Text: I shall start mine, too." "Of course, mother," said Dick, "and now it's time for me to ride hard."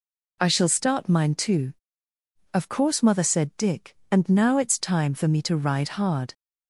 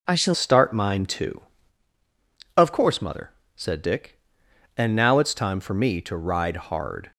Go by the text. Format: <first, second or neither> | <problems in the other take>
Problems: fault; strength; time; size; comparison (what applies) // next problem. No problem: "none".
first | changes voice at "start"; from 0.3 s on; 6.8 s long